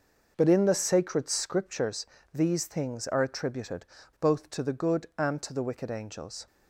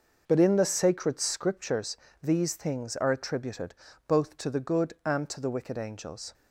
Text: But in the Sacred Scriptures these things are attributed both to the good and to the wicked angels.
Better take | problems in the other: neither | pauses between "Scriptures" and "these"; slight; the same in both // pauses between "attributed" and "both"; slight; the same in both

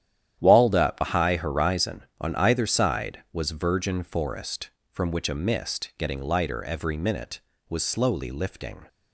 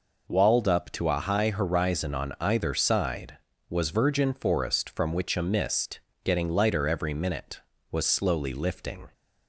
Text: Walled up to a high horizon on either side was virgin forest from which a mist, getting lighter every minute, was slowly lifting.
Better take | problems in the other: second | starts louder than the rest; strong; until 1.4 s; 10.5 dB // skips "to"; at 1.0 s

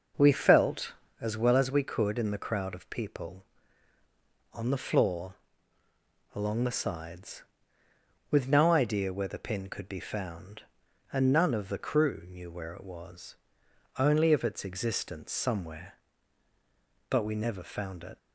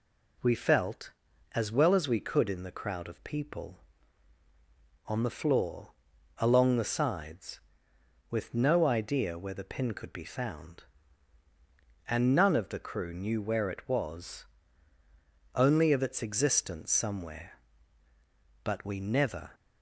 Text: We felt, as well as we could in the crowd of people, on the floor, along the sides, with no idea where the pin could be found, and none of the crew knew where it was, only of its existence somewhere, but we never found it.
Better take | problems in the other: first | stops before "found it"; at 19.5 s

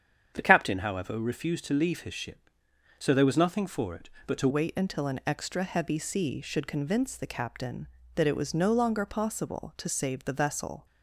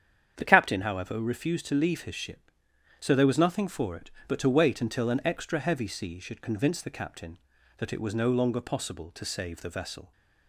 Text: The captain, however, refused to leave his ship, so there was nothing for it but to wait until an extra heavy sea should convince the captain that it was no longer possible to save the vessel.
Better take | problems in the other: second | starts louder than the rest; strong; until 1.3 s; 8 dB; strong in the second // changes voice at "wait"; from 4.4 s on; 6.4 s long

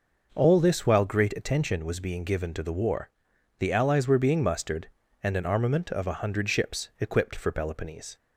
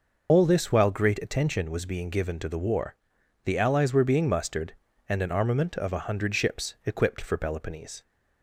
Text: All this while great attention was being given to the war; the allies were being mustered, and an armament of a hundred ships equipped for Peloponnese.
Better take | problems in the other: first | loses the start of "All"; at 0.2 s; 125 ms

